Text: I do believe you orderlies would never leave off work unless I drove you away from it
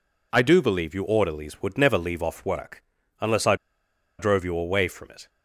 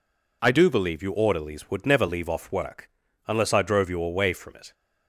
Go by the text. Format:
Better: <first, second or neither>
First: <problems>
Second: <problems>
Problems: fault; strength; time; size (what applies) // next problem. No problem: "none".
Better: second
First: pauses between "work" and "unless"; at 2.8 s; 0.38 s long // pauses between "I" and "drove"; noticeable; at 3.5 s; 0.64 s long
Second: pauses between "work" and "unless"; at 2.8 s; 0.38 s long